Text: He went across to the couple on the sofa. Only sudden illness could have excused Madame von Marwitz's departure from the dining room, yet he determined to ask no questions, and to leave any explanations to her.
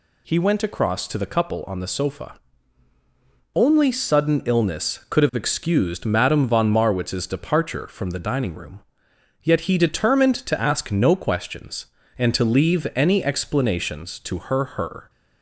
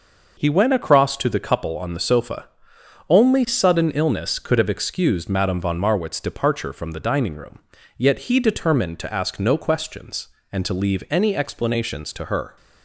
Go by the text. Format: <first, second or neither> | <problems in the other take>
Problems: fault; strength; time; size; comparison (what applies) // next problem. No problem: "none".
second | says "her" twice; at 14.7 s